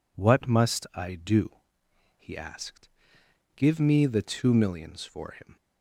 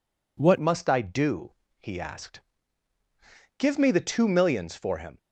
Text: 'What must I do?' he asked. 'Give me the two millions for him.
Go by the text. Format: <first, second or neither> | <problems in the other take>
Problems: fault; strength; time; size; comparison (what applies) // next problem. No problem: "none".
first | changes voice at "must"; from 0.5 s on; 4.6 s long